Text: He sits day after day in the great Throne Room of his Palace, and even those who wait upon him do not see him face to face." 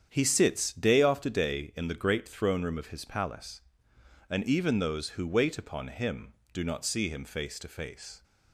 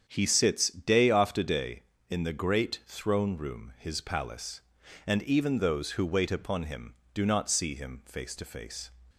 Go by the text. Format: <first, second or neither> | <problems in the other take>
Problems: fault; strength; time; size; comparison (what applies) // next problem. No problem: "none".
first | starts louder than the rest; strong; until 1.0 s; 7.5 dB; strong in the first // skips "of"; at 3.7 s